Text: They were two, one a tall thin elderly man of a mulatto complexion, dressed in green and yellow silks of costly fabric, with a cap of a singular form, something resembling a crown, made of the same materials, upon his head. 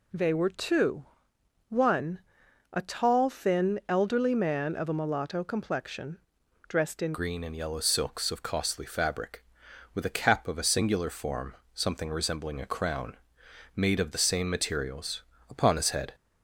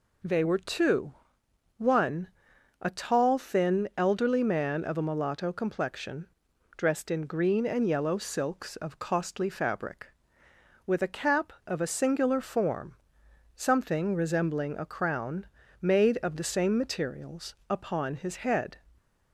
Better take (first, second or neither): second